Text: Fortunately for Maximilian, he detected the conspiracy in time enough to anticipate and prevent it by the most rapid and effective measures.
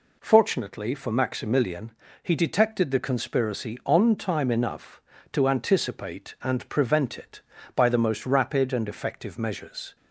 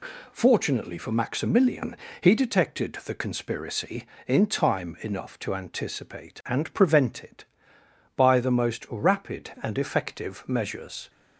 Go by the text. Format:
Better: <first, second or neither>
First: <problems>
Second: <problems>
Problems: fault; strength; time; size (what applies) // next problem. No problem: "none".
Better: second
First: says "on" for "in"; at 3.8 s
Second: none